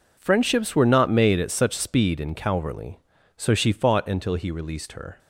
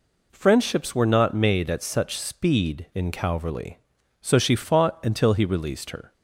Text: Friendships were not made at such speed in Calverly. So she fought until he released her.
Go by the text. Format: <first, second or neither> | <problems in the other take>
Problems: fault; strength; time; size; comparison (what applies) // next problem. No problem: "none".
neither | none